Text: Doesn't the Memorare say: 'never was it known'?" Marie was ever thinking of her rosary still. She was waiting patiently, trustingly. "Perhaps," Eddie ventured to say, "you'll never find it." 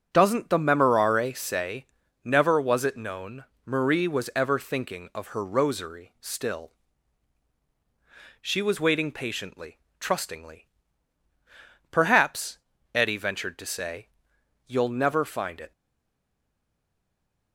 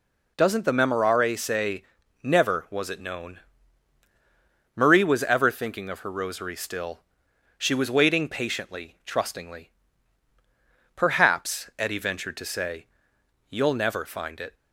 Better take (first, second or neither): second